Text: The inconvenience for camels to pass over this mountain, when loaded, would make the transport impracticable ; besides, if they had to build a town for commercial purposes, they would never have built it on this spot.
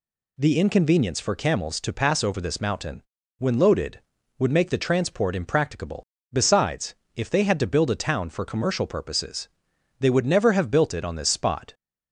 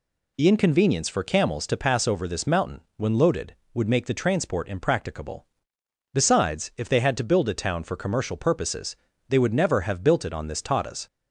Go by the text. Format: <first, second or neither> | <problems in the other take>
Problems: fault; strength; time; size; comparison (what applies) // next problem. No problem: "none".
first | says "tatas" for "spot"; at 10.6 s